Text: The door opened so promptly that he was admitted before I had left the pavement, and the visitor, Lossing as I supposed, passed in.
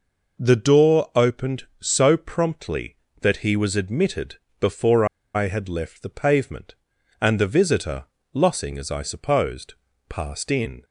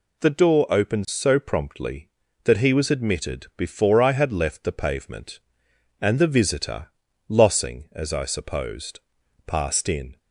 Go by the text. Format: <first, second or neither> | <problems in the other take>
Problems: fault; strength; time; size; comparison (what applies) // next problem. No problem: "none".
second | pauses between "admitted" and "before"; slight; at 4.3 s; 0.24 s long // pauses between "before" and "I"; slight; at 5.0 s; 0.29 s long